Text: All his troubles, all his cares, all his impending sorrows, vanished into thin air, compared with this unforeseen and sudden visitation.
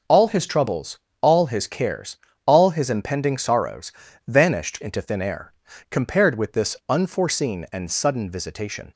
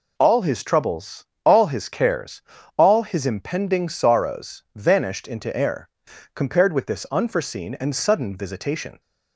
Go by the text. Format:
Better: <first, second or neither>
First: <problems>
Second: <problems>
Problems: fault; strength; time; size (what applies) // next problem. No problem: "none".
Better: first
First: none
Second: skips "thin"; at 5.5 s